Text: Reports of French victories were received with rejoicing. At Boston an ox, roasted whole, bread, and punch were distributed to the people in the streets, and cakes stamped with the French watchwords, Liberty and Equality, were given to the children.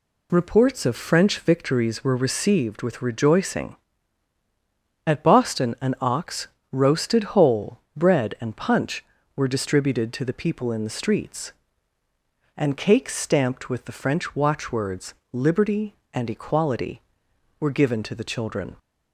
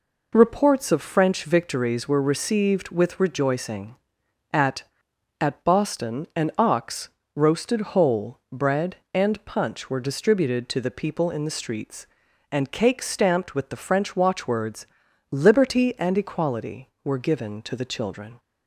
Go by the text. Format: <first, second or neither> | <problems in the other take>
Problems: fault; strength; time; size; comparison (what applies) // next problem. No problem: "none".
first | says "At" twice; at 5.3 s